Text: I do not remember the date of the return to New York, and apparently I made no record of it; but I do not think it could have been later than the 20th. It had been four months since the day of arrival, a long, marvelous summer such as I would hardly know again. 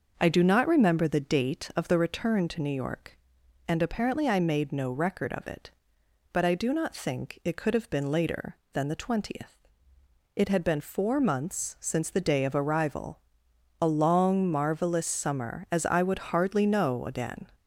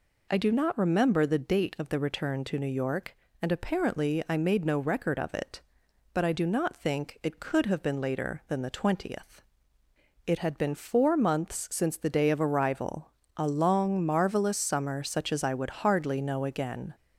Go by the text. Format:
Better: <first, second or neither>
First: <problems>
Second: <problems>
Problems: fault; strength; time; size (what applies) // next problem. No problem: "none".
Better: second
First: starts louder than the rest; noticeable; until 1.2 s; 6 dB // skips "such"; at 15.6 s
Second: none